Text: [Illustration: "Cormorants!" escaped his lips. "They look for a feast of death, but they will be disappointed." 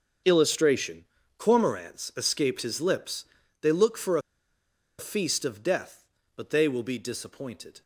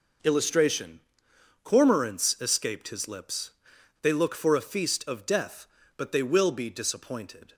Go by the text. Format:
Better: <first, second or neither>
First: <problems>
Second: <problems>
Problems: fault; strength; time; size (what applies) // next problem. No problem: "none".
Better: second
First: starts louder than the rest; until 1.5 s; 6.5 dB // pauses between "a" and "feast"; noticeable; at 4.2 s; 0.78 s long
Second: none